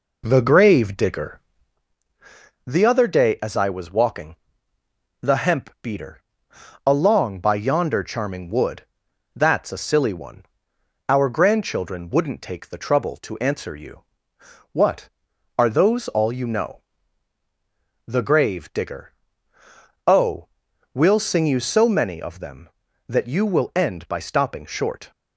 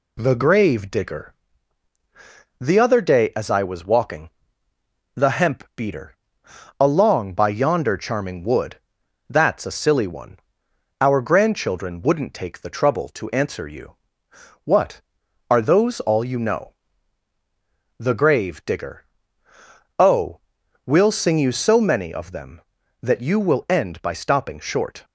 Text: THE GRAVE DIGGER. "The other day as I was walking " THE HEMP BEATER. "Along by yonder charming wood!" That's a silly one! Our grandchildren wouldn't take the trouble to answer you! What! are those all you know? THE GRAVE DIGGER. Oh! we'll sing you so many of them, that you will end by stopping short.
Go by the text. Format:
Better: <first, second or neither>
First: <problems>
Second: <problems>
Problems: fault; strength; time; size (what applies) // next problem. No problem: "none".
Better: second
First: starts louder than the rest; until 1.9 s; 4 dB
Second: none